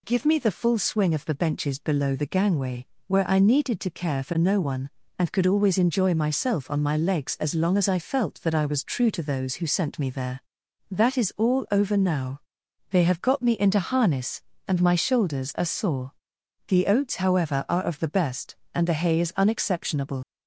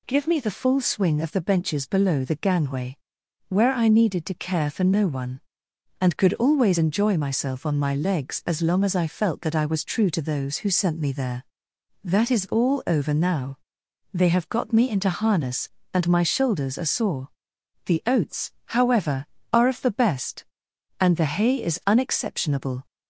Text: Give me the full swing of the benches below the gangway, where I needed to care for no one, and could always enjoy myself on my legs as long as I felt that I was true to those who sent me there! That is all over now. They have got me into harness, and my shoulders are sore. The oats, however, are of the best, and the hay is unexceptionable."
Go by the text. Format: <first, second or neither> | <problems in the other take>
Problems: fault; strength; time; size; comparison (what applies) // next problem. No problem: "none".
second | leaves "unexceptionable" unfinished; at 20.2 s; 55 ms